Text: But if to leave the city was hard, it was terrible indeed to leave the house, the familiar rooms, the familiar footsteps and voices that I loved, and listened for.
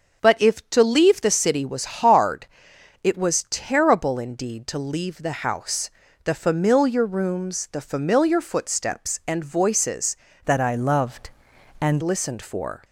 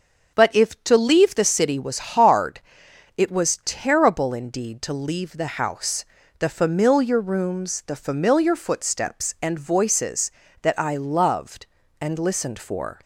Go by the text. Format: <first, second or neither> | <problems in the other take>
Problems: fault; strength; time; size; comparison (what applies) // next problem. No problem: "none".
second | starts louder than the rest; until 1.2 s; 6.5 dB; also in the second // changes voice from "that" to "and"; from 10.4 to 12.0 s; 1.6 s long